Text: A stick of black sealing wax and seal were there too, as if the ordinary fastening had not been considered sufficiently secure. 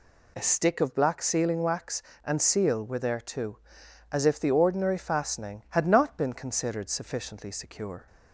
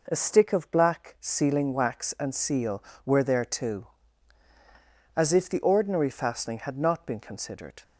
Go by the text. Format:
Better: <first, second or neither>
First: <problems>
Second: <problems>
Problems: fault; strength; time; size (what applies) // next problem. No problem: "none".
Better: first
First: none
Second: stops before "sufficiently secure"; at 7.8 s